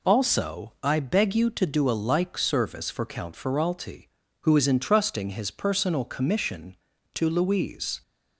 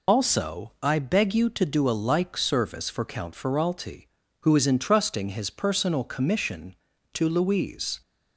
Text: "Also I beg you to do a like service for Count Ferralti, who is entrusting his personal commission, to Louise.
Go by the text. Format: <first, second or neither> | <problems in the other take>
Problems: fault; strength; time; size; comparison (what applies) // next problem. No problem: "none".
first | loses the start of "Also"; at 0.0 s; 50 ms